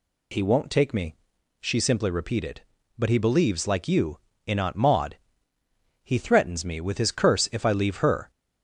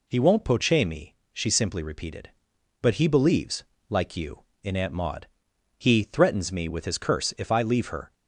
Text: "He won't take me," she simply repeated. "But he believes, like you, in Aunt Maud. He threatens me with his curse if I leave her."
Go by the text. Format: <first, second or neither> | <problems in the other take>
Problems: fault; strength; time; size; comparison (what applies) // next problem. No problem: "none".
first | says "poche" for "take"; at 0.4 s